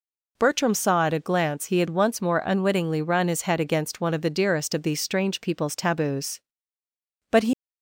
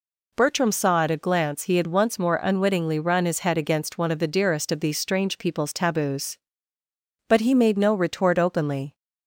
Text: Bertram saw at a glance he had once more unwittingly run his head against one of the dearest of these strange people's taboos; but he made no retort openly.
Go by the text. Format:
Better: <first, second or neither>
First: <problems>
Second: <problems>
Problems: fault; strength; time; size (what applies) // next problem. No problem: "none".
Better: second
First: stops before "made no retort openly"; at 7.5 s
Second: none